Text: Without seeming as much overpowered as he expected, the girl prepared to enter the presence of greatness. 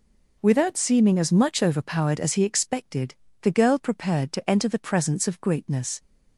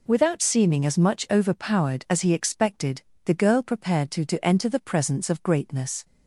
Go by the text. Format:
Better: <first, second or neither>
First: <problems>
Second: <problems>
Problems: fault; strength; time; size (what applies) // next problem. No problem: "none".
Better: first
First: none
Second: says "to" twice; at 4.2 s